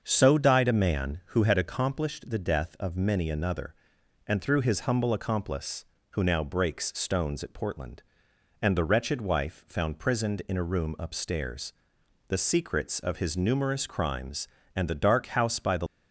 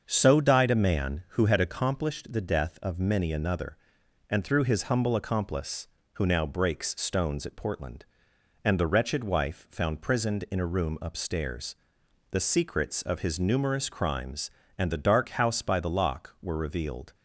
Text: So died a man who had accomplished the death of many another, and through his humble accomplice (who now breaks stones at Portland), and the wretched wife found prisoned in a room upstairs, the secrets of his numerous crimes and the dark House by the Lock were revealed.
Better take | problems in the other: second | starts louder than the rest; until 1.0 s; 6.5 dB; also in the second // stops before "Lock were revealed"; at 15.8 s

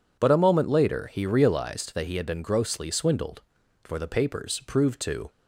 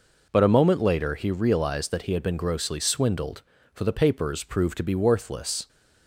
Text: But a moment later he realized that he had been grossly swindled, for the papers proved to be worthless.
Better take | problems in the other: second | stops before "be worthless"; at 5.2 s

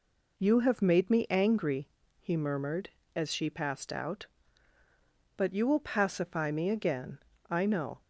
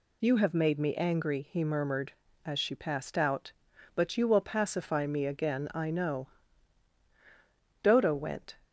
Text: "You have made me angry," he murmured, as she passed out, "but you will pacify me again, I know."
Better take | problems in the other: first | goes on to say "Dodo went"; noticeable; from 7.8 s on; 0.74 s long

